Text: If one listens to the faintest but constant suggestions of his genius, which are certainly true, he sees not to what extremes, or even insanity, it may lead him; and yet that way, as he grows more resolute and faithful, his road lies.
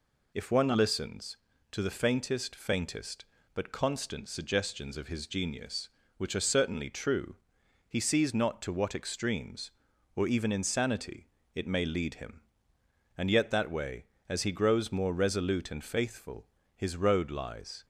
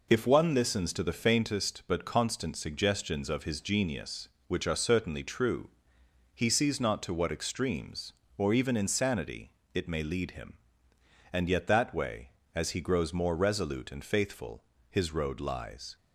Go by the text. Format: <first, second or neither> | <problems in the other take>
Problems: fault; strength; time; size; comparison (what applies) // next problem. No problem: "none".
second | says "faintest" twice; at 2.5 s